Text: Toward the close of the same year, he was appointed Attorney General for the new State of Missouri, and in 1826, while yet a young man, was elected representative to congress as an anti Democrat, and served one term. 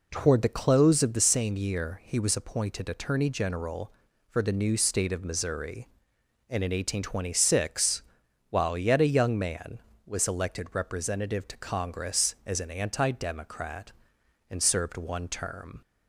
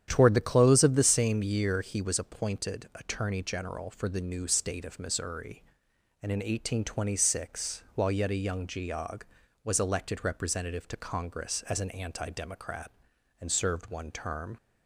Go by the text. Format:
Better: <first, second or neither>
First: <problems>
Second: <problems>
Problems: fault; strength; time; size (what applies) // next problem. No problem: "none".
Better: first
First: none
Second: starts louder than the rest; strong; until 1.0 s; 9.5 dB // says "geog" for "man"; at 8.6 s